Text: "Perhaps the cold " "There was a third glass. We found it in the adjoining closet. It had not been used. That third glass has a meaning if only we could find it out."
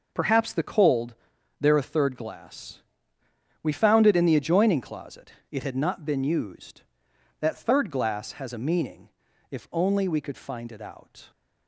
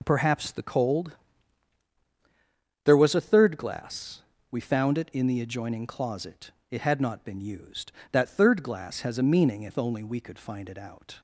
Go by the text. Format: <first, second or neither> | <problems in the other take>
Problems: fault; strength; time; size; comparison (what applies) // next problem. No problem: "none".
second | skips "was"; at 1.7 s // pauses between "meaning" and "if"; at 9.0 s; 0.42 s long